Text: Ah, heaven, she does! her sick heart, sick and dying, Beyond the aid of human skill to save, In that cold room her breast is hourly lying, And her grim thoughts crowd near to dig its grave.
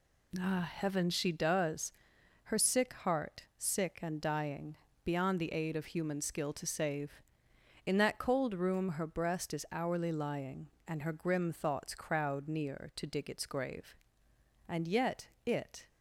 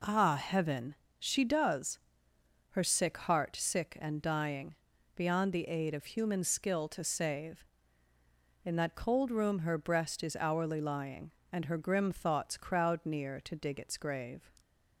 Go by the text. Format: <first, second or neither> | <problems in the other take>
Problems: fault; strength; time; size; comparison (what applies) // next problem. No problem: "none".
second | goes on to say "And yet it"; noticeable; from 14.6 s on; 1.2 s long